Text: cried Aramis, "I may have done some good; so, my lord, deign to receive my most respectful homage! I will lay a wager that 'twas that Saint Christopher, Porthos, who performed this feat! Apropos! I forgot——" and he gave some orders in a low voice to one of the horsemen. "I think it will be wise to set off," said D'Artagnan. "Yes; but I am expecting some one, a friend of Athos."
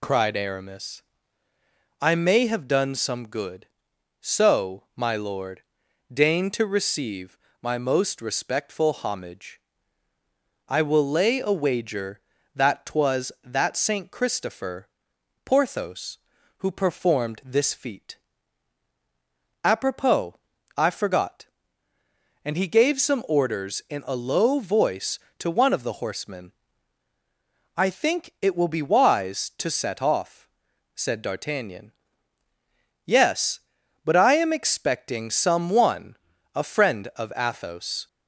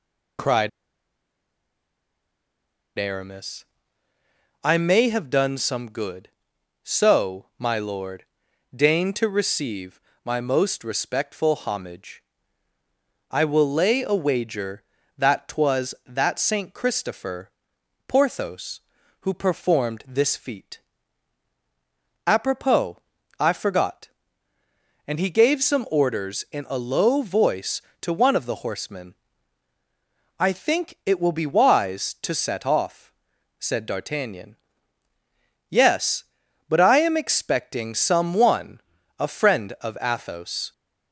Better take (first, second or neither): first